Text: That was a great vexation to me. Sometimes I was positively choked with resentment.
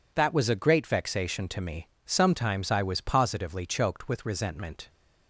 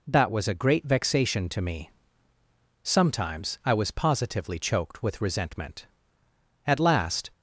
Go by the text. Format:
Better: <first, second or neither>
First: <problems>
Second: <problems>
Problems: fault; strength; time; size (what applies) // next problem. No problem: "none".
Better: first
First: none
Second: goes on to say "At last"; noticeable; from 6.6 s on; 0.66 s long